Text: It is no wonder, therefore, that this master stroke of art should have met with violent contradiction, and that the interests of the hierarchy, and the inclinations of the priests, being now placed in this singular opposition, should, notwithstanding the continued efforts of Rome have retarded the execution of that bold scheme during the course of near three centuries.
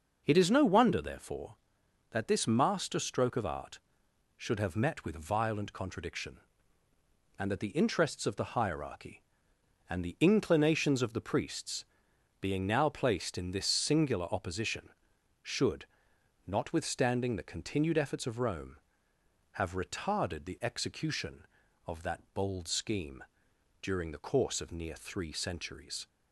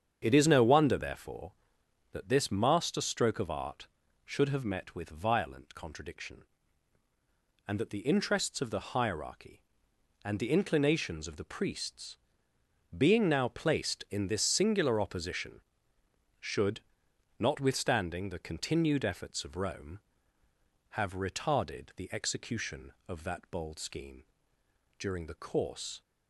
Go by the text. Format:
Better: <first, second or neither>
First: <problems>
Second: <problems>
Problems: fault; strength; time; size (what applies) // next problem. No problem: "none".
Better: first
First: pauses between "scheme" and "during"; noticeable; at 23.2 s; 0.58 s long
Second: starts louder than the rest; strong; until 1.2 s; 7.5 dB // pauses between "scheme" and "during"; noticeable; at 24.2 s; 0.78 s long // stops before "of near three centuries"; at 26.0 s